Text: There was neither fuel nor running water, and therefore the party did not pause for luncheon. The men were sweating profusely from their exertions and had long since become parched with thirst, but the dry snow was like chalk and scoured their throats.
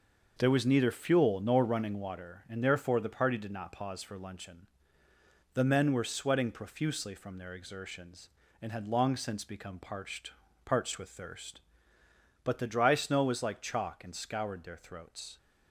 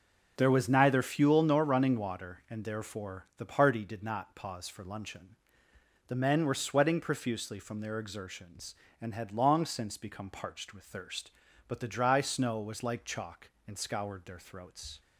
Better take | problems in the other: second | starts louder than the rest; noticeable; until 1.4 s; 6 dB // says "parched" twice; at 10.6 s

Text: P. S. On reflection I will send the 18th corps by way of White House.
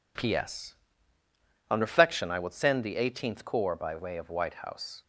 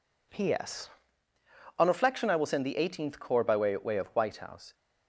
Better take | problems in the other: first | says "way" twice; at 3.7 s

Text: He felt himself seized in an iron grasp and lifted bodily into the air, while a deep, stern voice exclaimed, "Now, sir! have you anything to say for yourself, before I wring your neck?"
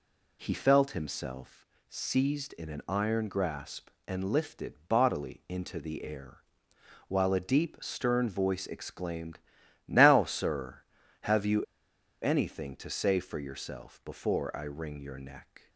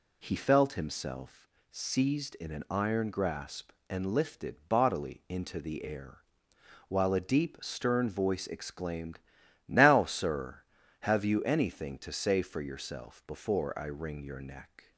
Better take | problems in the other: second | pauses between "himself" and "seized"; slight; at 1.6 s; 0.22 s long; slight in the second // pauses between "lifted" and "bodily"; slight; at 4.7 s; 0.16 s long; slight in the second // pauses between "you" and "anything"; noticeable; at 11.6 s; 0.59 s long

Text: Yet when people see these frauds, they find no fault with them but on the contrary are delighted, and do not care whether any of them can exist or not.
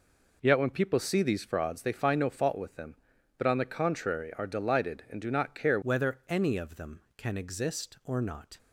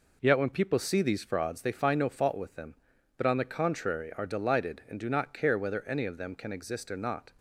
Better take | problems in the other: second | changes voice at "whether"; from 5.8 s on; 2.7 s long

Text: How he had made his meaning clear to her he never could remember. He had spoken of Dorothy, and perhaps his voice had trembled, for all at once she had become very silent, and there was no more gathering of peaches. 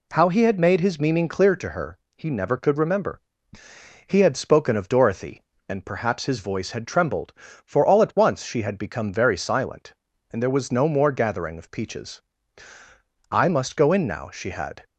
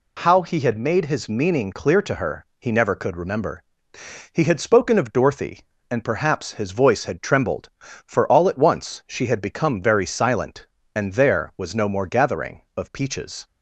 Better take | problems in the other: second | pauses between "her" and "he"; slight; at 1.9 s; 0.18 s long; slight in the second // goes on to say "I must go in now she had"; from 13.3 s on; 1.5 s long

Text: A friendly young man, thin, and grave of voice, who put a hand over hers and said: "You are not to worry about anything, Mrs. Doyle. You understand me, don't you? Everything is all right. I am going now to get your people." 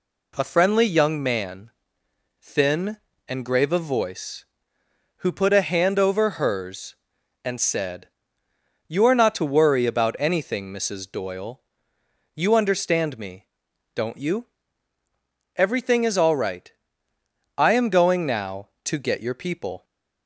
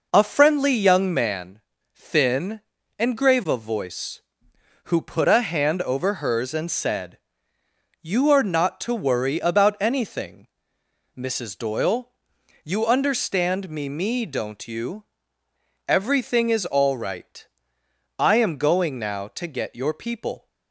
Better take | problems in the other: first | says "me" twice; at 13.8 s

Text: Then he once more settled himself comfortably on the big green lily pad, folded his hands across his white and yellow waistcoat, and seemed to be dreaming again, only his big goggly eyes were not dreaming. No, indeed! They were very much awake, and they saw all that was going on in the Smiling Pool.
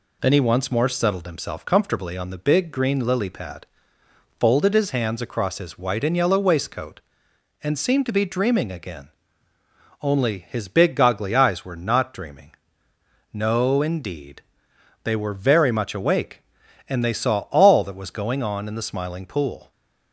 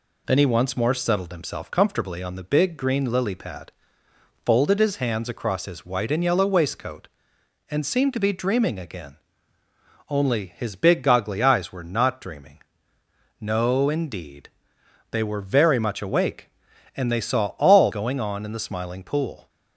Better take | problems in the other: first | skips "that was"; at 17.9 s

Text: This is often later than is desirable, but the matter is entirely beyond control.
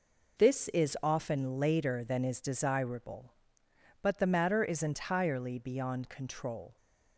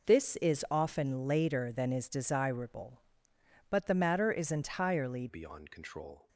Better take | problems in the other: first | changes voice at "beyond"; from 5.2 s on; 1.0 s long

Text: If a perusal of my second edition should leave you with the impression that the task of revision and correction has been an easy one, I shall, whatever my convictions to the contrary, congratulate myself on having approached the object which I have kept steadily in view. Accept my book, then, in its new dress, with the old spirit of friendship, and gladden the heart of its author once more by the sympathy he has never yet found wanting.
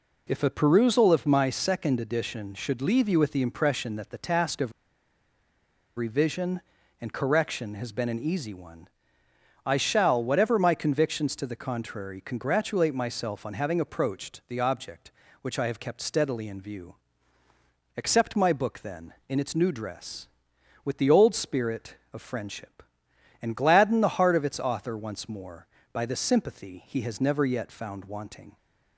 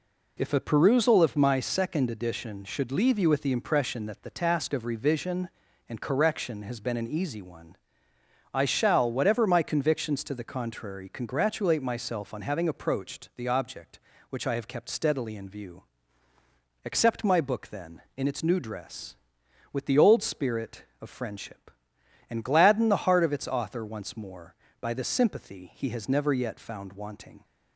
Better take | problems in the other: second | pauses between "of" and "revision"; strong; at 4.7 s; 1.2 s long

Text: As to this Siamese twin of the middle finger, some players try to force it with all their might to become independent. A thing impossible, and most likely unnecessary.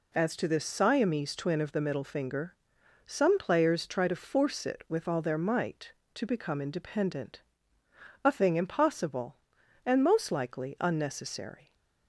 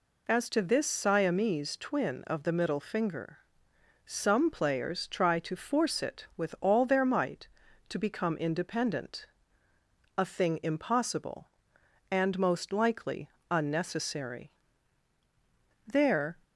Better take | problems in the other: first | pauses between "likely" and "unnecessary"; slight; at 13.2 s; 0.20 s long // goes on to say "There"; from 15.8 s on; 0.52 s long

